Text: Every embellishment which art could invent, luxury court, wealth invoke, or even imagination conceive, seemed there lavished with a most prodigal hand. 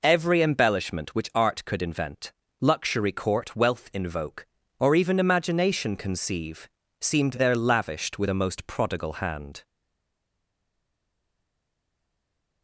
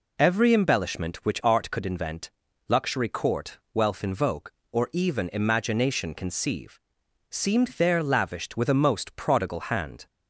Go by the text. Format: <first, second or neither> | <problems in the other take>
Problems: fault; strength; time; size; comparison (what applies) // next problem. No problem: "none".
second | stays silent after the last word; strong; from 9.6 s on; 3.0 s long